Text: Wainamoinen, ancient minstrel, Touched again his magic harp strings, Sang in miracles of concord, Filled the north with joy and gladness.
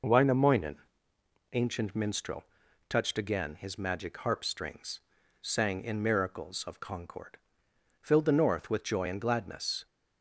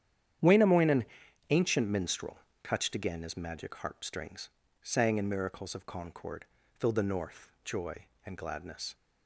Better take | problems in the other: first | starts louder than the rest; strong; until 1.8 s; 9.5 dB // skips "with"; at 7.5 s

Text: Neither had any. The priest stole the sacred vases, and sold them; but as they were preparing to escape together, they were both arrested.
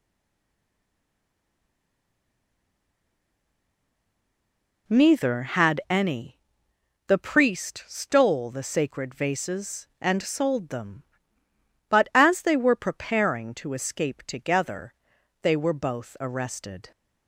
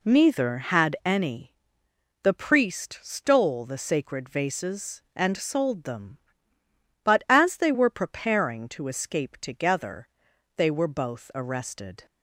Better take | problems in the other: second | stays silent before the first word; strong; until 4.8 s; 4.8 s long

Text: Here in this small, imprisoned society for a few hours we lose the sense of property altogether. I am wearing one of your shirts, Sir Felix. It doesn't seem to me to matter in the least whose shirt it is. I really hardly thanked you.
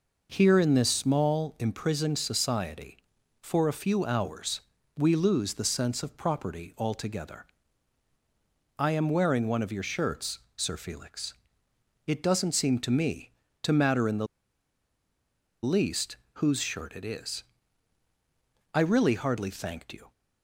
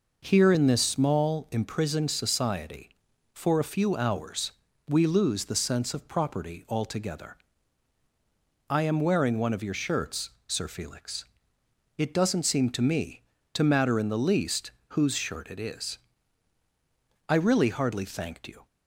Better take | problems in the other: second | pauses between "hours" and "we"; slight; at 4.6 s; 0.36 s long; slight in the second // pauses between "the" and "least"; strong; at 14.2 s; 1.3 s long // pauses between "least" and "whose"; slight; at 16.1 s; 0.20 s long; slight in the second

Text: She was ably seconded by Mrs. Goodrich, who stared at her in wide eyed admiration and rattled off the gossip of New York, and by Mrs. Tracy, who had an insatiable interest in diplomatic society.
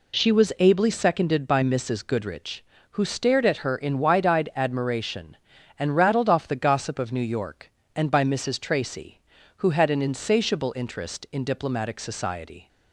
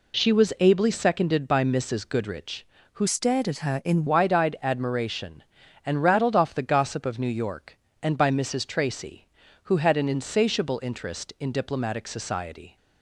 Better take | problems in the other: first | changes voice from "stared" to "in"; from 3.0 to 4.0 s; 1.0 s long

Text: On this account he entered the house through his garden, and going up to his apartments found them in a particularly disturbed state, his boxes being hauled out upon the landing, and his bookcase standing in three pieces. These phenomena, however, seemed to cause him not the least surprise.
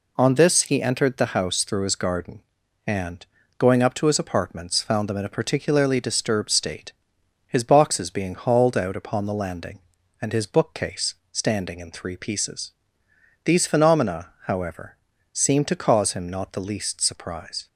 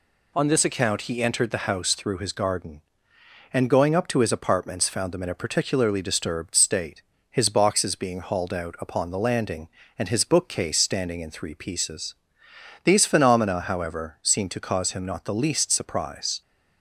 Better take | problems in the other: second | skips "account"; at 0.6 s // pauses between "and" and "going"; slight; at 3.2 s; 0.32 s long // pauses between "bookcase" and "standing"; slight; at 11.1 s; 0.16 s long

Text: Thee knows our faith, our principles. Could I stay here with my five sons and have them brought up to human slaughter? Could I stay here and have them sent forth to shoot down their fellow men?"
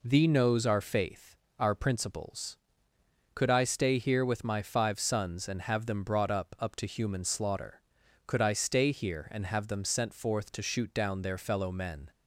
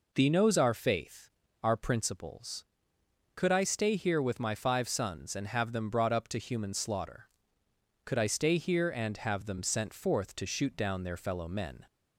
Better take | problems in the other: second | says "up" twice; at 6.5 s

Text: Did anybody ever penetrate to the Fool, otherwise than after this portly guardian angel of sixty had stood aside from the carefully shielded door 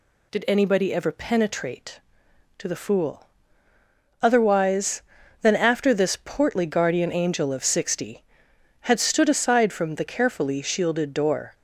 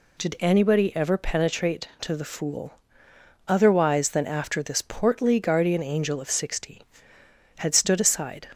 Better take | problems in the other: first | stops before "from the carefully shielded door"; at 8.5 s

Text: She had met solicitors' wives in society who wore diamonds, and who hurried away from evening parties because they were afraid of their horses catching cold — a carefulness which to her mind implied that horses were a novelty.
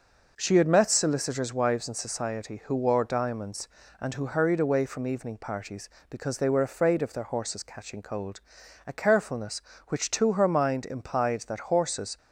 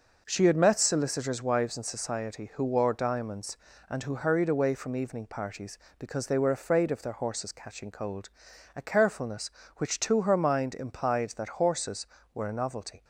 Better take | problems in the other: second | stops before "were a novelty"; at 12.1 s

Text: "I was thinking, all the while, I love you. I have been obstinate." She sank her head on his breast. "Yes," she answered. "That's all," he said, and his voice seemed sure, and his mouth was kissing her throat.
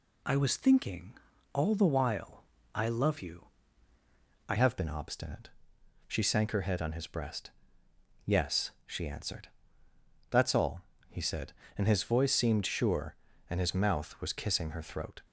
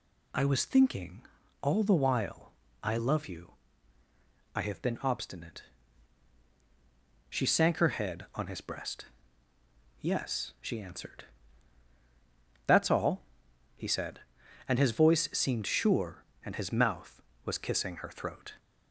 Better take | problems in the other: second | changes voice at "have"; from 4.5 s on; 10.6 s long

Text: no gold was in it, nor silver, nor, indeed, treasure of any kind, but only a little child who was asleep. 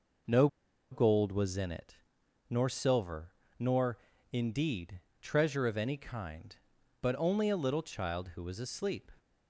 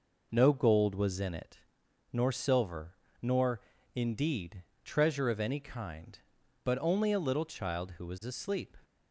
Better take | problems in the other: second | pauses between "no" and "gold"; at 0.4 s; 0.44 s long

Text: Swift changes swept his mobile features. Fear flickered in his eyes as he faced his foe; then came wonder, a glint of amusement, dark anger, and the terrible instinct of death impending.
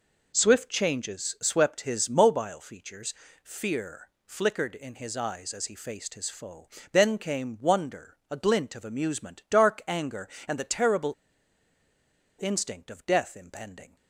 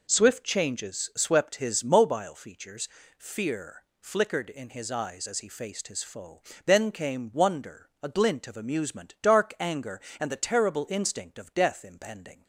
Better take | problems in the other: second | pauses between "Fear" and "flickered"; slight; at 4.0 s; 0.18 s long; slight in the second // pauses between "terrible" and "instinct"; strong; at 11.1 s; 1.2 s long

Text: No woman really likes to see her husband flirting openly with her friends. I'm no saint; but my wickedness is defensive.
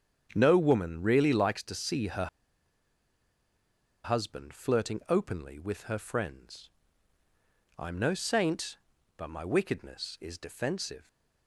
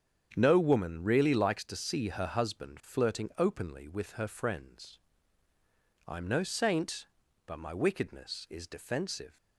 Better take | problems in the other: second | starts louder than the rest; strong; until 1.3 s; 8 dB; strong in the second // pauses between "her" and "husband"; strong; at 2.2 s; 1.7 s long

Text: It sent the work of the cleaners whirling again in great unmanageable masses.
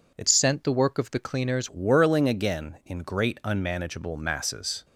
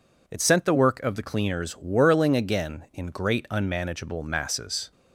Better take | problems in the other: second | changes voice from "sent" to "cleaners"; from 0.2 to 1.6 s; 1.4 s long

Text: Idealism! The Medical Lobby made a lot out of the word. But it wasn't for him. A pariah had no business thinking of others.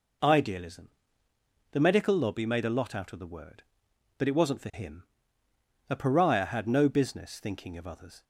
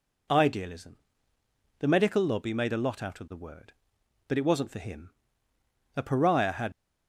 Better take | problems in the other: first | stops before "no business thinking of others"; at 6.7 s

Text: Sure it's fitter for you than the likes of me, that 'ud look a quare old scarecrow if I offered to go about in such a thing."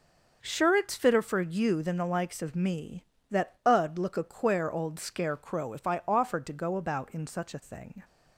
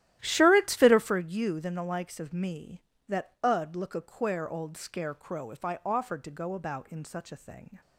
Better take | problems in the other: first | starts louder than the rest; strong; until 1.2 s; 13.5 dB

